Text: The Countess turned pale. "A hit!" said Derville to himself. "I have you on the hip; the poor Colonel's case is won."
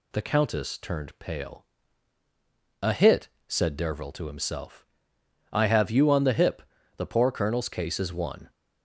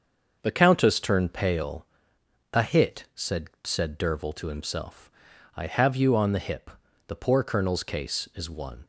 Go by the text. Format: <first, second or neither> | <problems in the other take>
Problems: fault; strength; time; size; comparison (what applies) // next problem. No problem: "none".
first | starts louder than the rest; until 1.4 s; 6.5 dB // says "said" twice; at 3.6 s